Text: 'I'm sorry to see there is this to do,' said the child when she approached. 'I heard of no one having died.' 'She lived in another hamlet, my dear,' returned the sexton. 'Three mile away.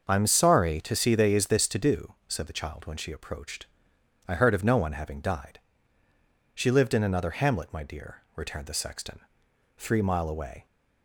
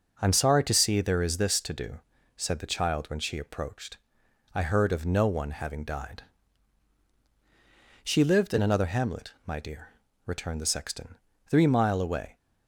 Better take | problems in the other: second | starts louder than the rest; until 1.0 s; 6.5 dB // says "they" for "there"; at 1.1 s

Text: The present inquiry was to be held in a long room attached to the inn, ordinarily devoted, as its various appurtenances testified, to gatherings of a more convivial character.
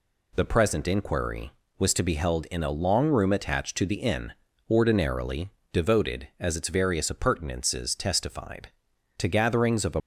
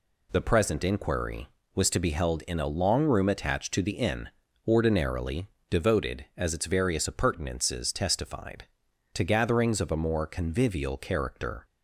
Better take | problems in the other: second | pauses between "ordinarily" and "devoted"; slight; at 5.5 s; 0.22 s long; slight in the second // stops before "more convivial character"; at 10.0 s

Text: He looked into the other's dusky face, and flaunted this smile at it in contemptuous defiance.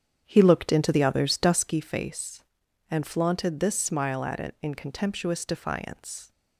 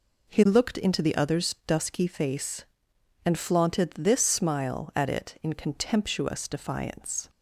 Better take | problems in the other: second | starts louder than the rest; strong; until 1.8 s; 8.5 dB

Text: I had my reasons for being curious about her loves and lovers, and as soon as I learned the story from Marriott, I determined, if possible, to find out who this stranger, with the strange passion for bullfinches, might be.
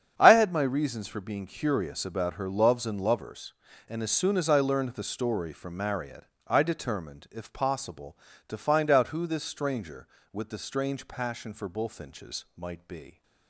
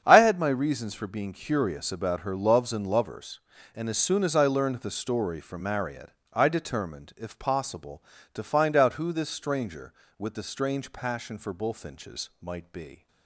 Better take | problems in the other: neither | starts louder than the rest; strong; the same in both

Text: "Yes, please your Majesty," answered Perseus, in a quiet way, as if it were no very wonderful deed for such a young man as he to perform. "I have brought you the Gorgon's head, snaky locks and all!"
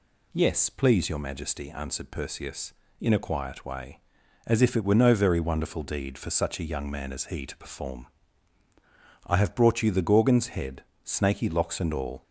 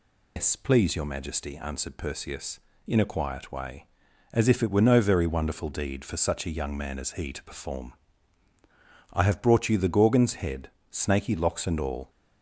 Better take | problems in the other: first | loses the start of "Yes"; at 0.3 s; 165 ms

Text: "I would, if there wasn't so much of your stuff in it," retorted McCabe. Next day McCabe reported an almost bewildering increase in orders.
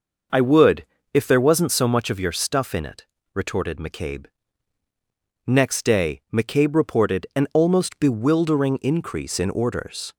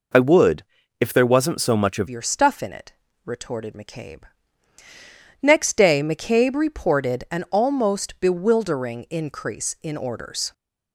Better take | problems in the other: first | changes voice at "your"; from 2.0 s on; 8.5 s long

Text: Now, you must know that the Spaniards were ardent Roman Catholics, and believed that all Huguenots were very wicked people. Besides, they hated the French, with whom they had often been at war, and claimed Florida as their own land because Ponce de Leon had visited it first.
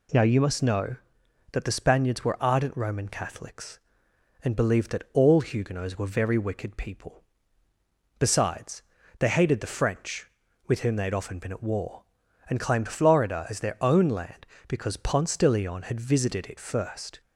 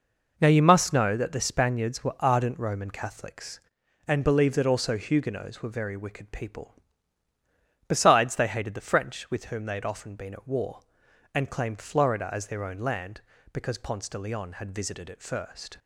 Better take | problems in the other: first | says "also" for "all"; at 4.6 s

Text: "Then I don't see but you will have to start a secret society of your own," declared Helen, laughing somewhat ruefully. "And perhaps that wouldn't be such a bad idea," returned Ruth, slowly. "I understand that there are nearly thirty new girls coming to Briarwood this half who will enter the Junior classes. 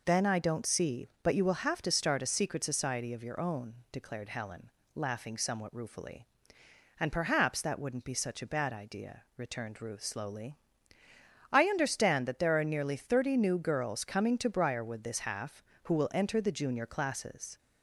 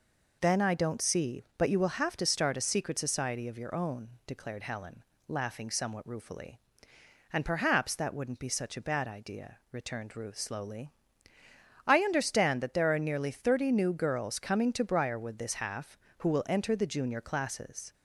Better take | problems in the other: neither | none

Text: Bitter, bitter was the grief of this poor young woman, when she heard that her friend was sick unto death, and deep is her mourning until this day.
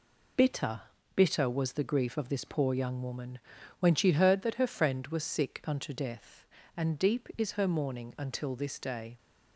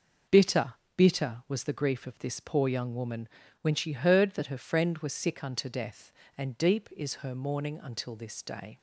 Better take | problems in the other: neither | none

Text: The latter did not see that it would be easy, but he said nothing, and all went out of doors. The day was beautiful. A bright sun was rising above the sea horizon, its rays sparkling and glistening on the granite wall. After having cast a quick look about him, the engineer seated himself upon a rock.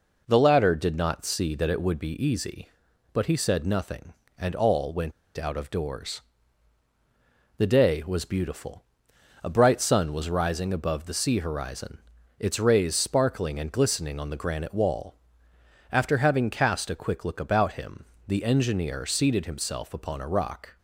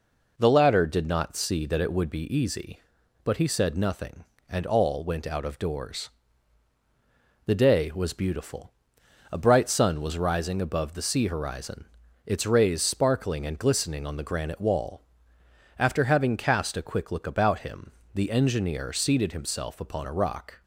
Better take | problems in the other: second | pauses between "went" and "out"; slight; at 5.1 s; 0.25 s long

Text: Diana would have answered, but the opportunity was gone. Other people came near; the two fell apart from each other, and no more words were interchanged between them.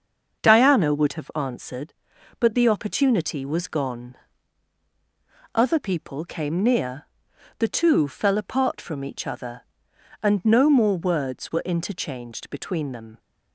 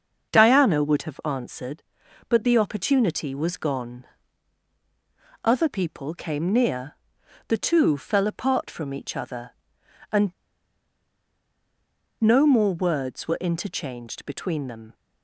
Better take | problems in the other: first | starts louder than the rest; until 1.3 s; 6.5 dB; also in the first // pauses between "and" and "no"; strong; at 10.2 s; 1.9 s long

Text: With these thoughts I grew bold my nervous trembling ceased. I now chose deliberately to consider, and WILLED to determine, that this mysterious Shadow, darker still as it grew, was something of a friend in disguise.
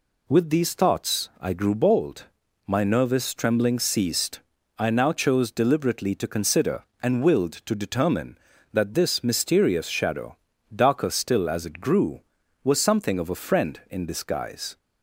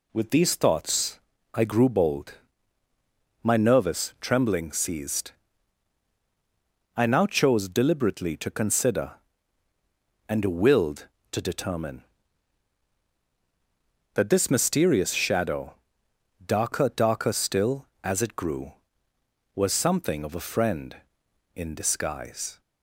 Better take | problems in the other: first | pauses between "thoughts" and "I"; slight; at 1.2 s; 0.32 s long // pauses between "bold" and "my"; at 2.3 s; 1.1 s long; also in the first // says "darker" twice; at 16.9 s

